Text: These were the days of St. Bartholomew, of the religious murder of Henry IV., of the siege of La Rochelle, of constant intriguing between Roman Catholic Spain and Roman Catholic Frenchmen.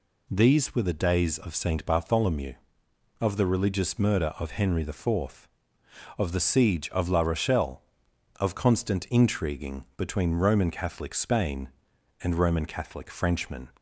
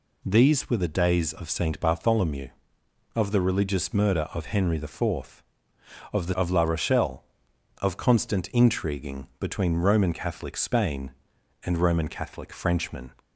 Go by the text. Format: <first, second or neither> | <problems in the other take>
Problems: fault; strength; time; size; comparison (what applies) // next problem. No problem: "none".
first | skips "siege"; at 6.3 s